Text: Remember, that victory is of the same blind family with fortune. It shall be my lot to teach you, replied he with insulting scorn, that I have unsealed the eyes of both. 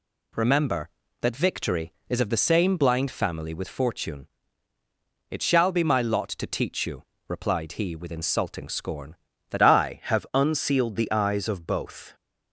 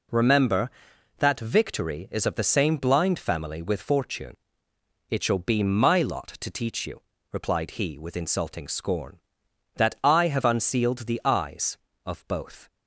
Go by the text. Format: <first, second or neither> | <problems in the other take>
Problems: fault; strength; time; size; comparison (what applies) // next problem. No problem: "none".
second | changes voice at "I"; from 9.6 s on; 2.5 s long